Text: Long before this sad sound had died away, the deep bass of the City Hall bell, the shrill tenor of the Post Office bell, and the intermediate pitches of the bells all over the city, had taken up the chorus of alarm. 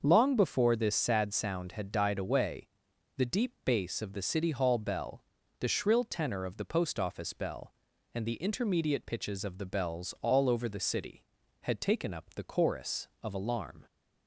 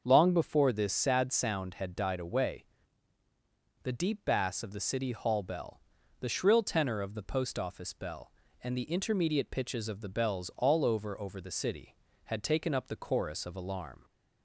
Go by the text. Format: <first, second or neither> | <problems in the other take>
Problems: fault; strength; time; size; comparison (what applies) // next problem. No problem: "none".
first | starts louder than the rest; until 1.0 s; 6.5 dB; also in the first // says "over" twice; at 11.1 s